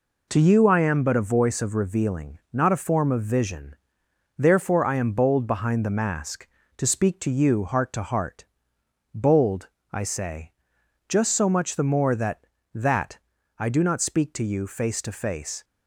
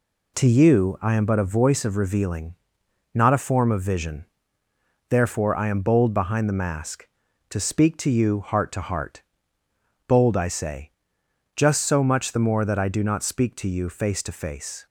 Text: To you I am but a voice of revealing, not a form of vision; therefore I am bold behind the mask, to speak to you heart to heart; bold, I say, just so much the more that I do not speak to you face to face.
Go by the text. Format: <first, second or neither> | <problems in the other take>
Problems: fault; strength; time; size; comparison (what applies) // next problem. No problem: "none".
second | says "that" twice; at 12.7 s